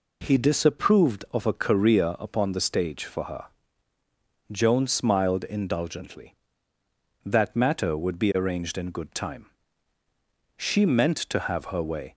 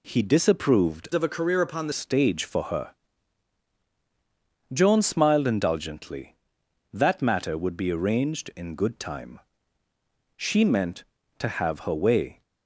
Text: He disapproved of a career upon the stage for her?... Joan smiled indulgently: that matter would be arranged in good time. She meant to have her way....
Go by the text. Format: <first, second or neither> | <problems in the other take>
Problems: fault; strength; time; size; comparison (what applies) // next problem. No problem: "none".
first | changes voice from "of" to "the"; from 1.1 to 1.9 s; 0.8 s long